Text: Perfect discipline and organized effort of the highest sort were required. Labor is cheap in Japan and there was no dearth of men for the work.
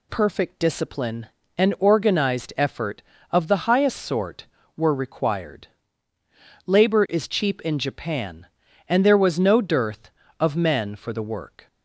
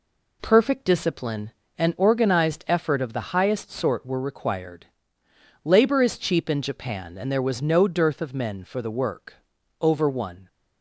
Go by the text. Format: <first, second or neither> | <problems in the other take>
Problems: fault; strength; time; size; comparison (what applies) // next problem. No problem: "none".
first | goes on to say "Over one"; noticeable; from 9.8 s on; 0.66 s long